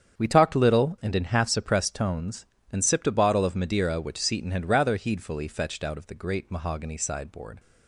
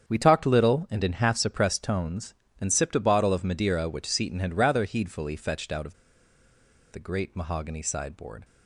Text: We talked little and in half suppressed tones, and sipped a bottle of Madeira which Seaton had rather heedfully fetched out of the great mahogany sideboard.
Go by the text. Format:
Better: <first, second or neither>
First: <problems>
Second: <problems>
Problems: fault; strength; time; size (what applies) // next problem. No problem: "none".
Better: first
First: starts louder than the rest; strong; until 1.2 s; 8 dB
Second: starts louder than the rest; strong; until 1.1 s; 8 dB // pauses between "of" and "the"; noticeable; at 5.9 s; 0.97 s long